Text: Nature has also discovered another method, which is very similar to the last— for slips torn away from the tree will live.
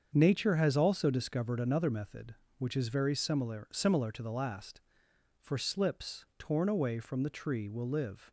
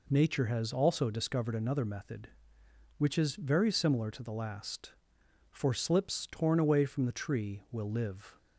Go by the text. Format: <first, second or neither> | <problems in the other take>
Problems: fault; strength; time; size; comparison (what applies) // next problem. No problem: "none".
second | starts louder than the rest; until 1.1 s; 7 dB // says "similar" twice; at 3.7 s